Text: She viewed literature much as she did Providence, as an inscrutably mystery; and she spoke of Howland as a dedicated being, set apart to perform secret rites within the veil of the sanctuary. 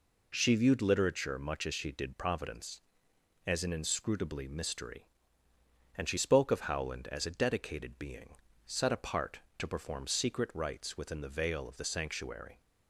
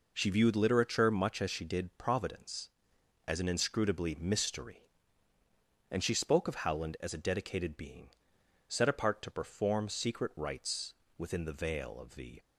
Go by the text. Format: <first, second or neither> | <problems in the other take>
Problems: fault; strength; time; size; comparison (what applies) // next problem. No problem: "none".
first | pauses between "rites" and "within"; slight; at 10.9 s; 0.24 s long // stops before "sanctuary"; at 12.3 s